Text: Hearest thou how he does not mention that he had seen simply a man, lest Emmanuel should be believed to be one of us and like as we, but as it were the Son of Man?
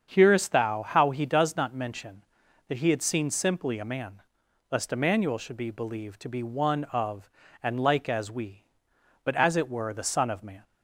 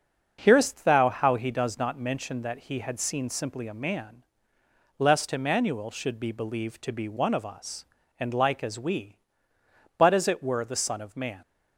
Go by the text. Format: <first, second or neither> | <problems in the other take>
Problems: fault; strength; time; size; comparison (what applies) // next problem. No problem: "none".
second | starts louder than the rest; strong; until 1.1 s; 7.5 dB; also in the second // skips "us"; at 7.4 s